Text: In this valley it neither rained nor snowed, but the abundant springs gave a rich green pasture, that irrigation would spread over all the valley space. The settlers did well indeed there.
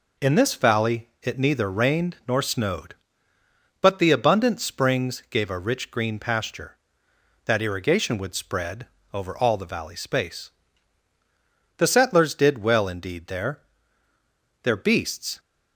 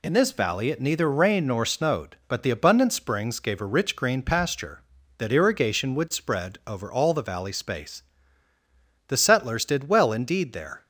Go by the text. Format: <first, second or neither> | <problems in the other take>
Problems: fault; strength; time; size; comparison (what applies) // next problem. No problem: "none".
second | pauses between "spread" and "over"; slight; at 8.8 s; 0.26 s long // goes on to say "Their beasts"; noticeable; from 14.6 s on; 0.76 s long